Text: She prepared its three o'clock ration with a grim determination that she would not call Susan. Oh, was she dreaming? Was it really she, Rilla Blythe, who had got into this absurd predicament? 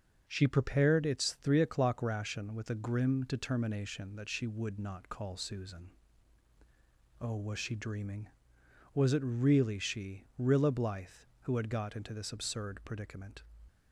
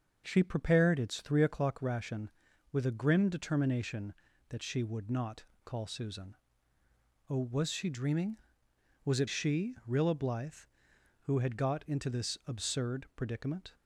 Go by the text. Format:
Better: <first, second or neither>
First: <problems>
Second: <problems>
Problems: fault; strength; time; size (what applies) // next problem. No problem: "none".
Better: first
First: starts louder than the rest; until 1.2 s; 7 dB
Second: starts louder than the rest; until 1.2 s; 6.5 dB // pauses between "not" and "call"; slight; at 5.4 s; 0.20 s long // skips "really"; at 9.2 s